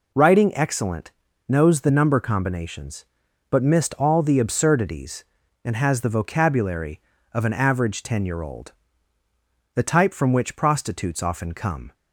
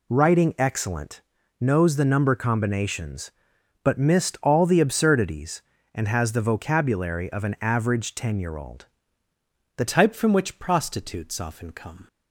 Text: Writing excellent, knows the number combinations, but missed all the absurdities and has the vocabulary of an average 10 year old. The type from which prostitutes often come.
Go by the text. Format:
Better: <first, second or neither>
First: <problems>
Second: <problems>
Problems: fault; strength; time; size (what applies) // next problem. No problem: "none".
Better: first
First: none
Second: changes voice at "type"; from 9.8 s on; 2.2 s long